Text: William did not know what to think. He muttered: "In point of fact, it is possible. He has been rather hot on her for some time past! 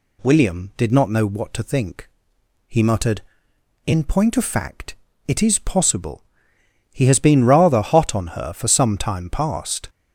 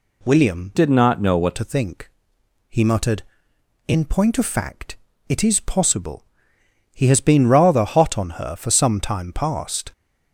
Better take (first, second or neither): first